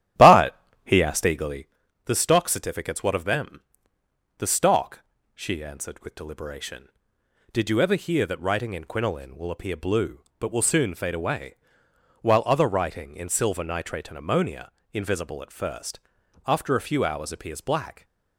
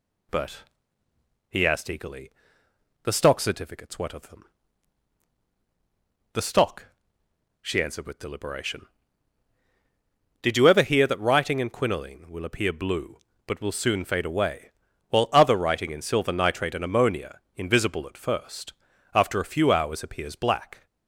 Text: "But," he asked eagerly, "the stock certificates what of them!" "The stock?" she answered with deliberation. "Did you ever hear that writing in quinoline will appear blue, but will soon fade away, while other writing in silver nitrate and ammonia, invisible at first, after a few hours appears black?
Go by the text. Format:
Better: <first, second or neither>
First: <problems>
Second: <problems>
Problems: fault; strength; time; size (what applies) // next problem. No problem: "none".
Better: second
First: starts louder than the rest; strong; until 1.7 s; 12 dB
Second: none